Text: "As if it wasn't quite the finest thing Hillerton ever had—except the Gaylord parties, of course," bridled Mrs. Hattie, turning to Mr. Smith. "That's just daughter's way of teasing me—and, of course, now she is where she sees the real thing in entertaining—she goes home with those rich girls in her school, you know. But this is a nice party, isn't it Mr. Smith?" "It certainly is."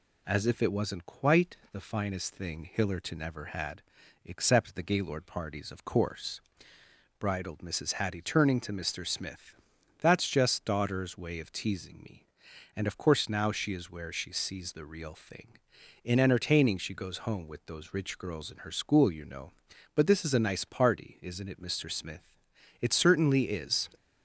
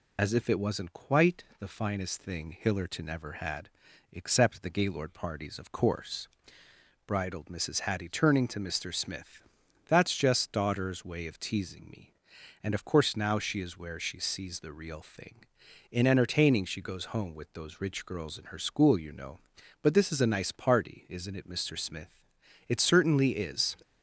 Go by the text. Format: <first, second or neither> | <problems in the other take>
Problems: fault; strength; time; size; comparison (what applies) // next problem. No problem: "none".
first | loses the start of "As"; at 0.1 s; 45 ms